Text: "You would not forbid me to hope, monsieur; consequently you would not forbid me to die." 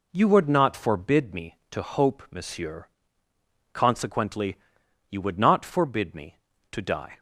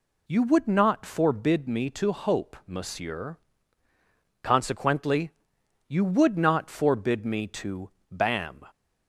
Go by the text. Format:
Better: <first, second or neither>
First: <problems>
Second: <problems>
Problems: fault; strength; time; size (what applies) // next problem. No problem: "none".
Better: first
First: pauses between "consequently" and "you"; noticeable; at 4.5 s; 0.56 s long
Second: pauses between "consequently" and "you"; noticeable; at 5.3 s; 0.56 s long // says "bam" for "die"; at 8.1 s